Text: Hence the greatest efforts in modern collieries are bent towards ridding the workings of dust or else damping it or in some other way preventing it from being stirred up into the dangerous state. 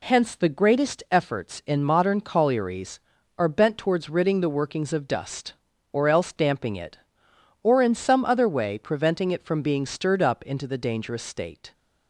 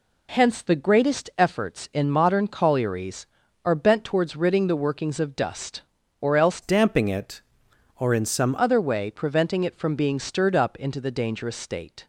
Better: first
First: none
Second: changes voice from "damping" to "some"; from 6.6 to 8.5 s; 1.9 s long

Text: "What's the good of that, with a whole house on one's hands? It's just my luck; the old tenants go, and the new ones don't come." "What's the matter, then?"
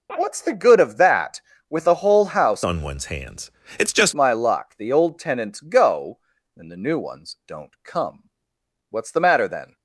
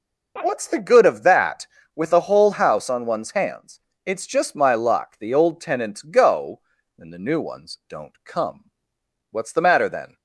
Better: second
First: changes voice from "on" to "just"; from 2.6 to 4.1 s; 1.5 s long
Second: none

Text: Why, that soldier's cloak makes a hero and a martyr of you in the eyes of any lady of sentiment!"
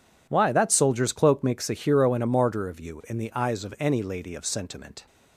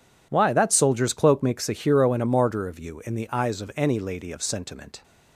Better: neither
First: none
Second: none

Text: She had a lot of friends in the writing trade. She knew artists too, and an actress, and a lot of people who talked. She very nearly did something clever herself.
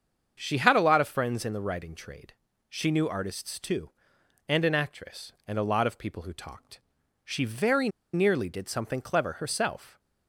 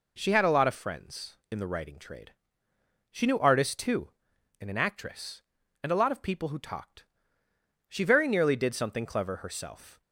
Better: second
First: starts louder than the rest; until 1.4 s; 7 dB // pauses between "very" and "nearly"; slight; at 7.8 s; 0.25 s long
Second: none

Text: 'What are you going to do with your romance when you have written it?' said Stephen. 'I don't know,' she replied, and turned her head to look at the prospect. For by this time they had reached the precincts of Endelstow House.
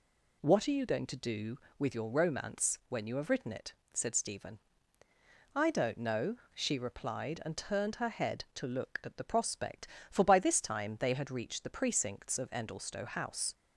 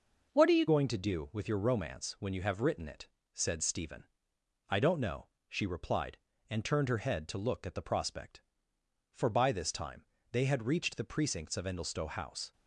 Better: first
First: none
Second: changes voice at "going"; from 0.6 s on; 11.9 s long // pauses between "time" and "they"; slight; at 10.0 s; 0.28 s long

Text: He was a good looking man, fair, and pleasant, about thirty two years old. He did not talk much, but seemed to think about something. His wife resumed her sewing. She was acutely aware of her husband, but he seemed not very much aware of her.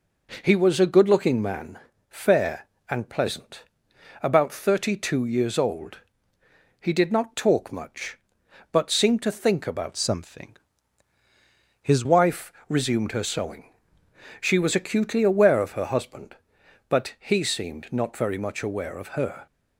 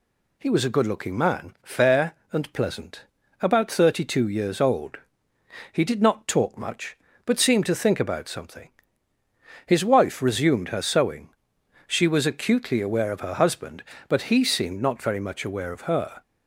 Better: second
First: changes voice from "something" to "His"; from 9.9 to 12.0 s; 2.1 s long // pauses between "wife" and "resumed"; slight; at 12.5 s; 0.16 s long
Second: none

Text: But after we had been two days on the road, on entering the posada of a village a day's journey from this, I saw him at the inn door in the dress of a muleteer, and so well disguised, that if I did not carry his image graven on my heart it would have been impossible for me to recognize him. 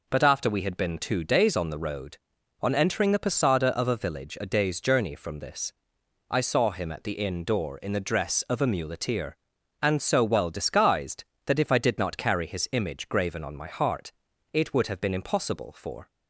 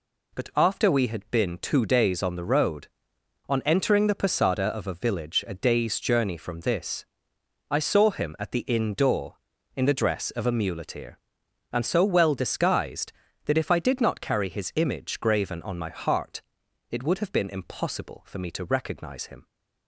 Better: second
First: pauses between "heart" and "it"; at 14.1 s; 0.40 s long // stops before "me to recognize him"; at 16.0 s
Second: pauses between "heart" and "it"; noticeable; at 16.3 s; 0.50 s long

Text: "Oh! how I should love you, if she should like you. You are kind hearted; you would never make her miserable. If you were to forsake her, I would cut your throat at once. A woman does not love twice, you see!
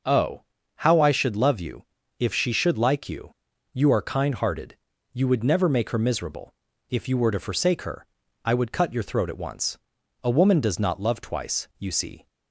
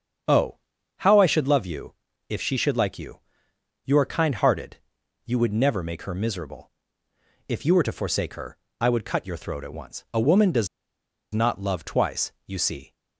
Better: first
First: none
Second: starts louder than the rest; strong; until 1.6 s; 7.5 dB // pauses between "does" and "not"; noticeable; at 10.6 s; 0.65 s long

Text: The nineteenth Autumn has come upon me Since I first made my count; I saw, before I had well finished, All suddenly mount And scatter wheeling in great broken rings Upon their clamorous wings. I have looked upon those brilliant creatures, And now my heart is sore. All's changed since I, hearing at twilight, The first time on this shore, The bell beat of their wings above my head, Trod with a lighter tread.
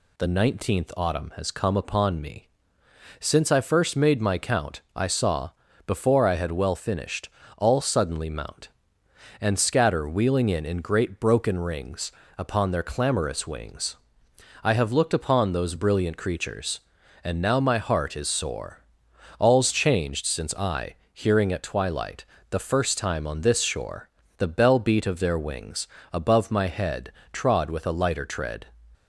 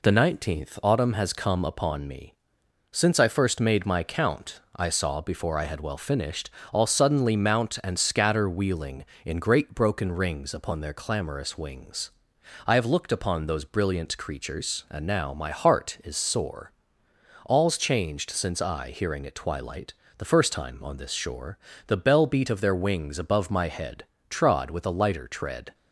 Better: second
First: pauses between "me" and "Since"; noticeable; at 2.4 s; 0.70 s long // says "in" twice; at 10.6 s // pauses between "rings" and "Upon"; slight; at 12.1 s; 0.26 s long // pauses between "wings" and "above"; slight; at 25.8 s; 0.24 s long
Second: pauses between "me" and "Since"; noticeable; at 2.3 s; 0.58 s long

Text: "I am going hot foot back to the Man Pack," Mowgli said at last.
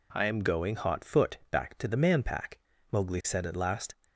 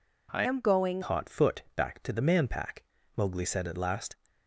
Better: first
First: none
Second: changes voice from "am" to "going"; from 0.4 to 1.0 s; 0.6 s long

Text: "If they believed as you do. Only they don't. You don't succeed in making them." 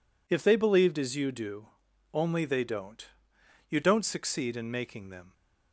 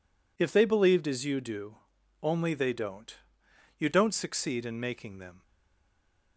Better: first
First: none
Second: stays silent after the last word; from 5.4 s on; 0.9 s long

